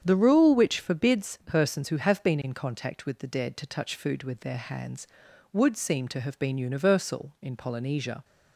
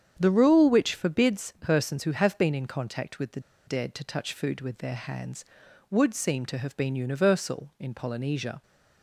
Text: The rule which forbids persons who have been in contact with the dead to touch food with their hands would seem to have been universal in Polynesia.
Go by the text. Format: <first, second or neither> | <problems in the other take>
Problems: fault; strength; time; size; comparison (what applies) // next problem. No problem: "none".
first | starts louder than the rest; strong; until 1.2 s; 8 dB; strong in the first // pauses between "the" and "dead"; slight; at 3.3 s; 0.27 s long